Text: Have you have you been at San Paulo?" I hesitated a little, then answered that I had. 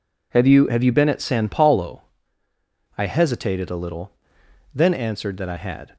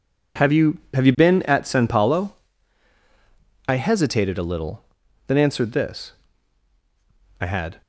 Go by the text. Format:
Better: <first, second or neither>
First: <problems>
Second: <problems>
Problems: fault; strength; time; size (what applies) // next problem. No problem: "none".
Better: first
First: none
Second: says "this" for "that"; at 5.7 s